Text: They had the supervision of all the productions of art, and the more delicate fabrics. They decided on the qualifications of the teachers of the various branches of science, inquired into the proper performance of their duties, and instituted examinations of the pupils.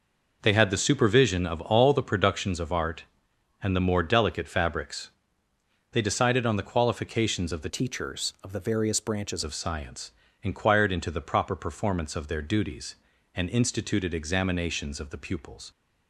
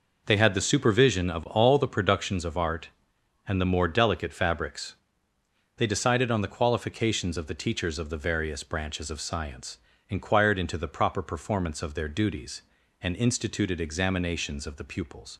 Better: second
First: changes voice from "teachers" to "branches"; from 7.6 to 9.4 s; 1.8 s long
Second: none

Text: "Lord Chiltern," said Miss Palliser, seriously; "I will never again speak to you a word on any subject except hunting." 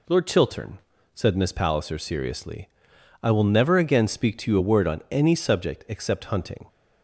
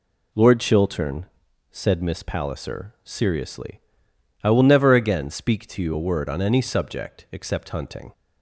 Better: neither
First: none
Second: none

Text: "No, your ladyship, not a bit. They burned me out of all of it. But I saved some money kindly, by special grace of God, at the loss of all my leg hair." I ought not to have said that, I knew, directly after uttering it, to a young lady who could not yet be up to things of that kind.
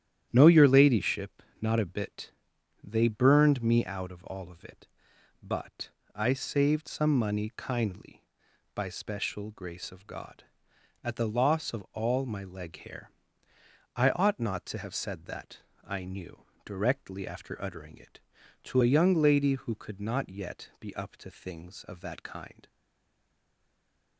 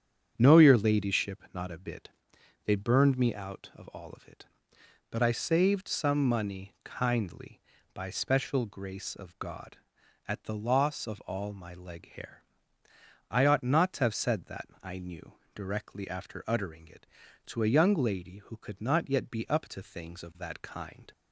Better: second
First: starts louder than the rest; strong; until 1.3 s; 10.5 dB // pauses between "But" and "I"; slight; at 5.8 s; 0.26 s long // stays silent after the last word; noticeable; from 22.6 s on; 1.5 s long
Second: starts louder than the rest; strong; until 1.3 s; 8.5 dB

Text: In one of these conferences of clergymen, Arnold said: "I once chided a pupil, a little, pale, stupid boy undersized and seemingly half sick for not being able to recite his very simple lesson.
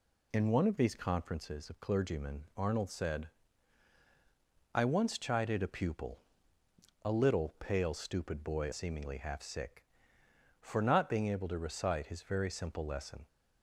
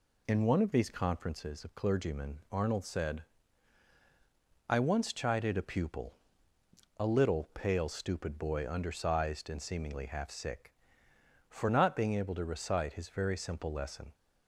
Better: second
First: skips "undersized and"; at 8.7 s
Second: none

